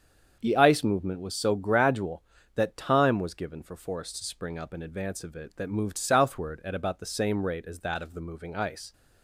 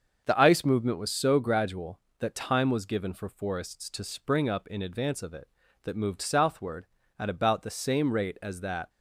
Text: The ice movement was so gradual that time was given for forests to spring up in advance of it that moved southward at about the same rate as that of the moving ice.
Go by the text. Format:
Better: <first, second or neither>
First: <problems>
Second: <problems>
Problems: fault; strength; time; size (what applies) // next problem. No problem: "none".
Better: first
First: starts louder than the rest; until 1.4 s; 7 dB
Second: starts louder than the rest; until 1.2 s; 6.5 dB // stops before "of the moving ice"; at 8.8 s